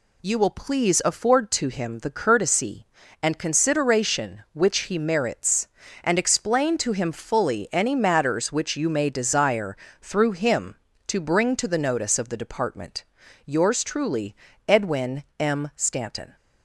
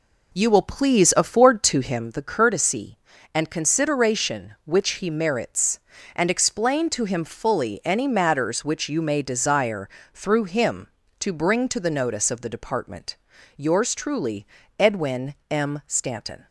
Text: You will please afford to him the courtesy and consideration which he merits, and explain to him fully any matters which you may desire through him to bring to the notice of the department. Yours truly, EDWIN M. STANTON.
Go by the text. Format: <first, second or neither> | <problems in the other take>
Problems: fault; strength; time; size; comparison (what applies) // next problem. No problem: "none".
first | starts louder than the rest; until 2.2 s; 3.5 dB // pauses between "desire" and "through"; slight; at 9.8 s; 0.24 s long; slight in the first // pauses between "EDWIN" and "M"; slight; at 15.3 s; 0.16 s long; slight in the first